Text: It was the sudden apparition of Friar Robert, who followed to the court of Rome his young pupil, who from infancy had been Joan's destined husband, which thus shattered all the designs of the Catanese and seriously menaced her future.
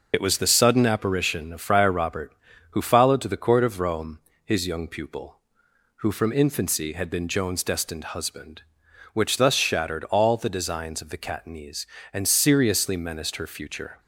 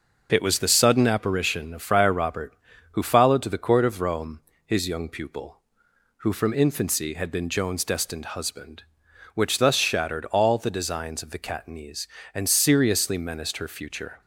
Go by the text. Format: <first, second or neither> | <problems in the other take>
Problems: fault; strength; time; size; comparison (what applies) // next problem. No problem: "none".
second | loses the start of "It"; at 0.1 s; 50 ms // pauses between "Rome" and "his"; slight; at 4.1 s; 0.26 s long; slight in the second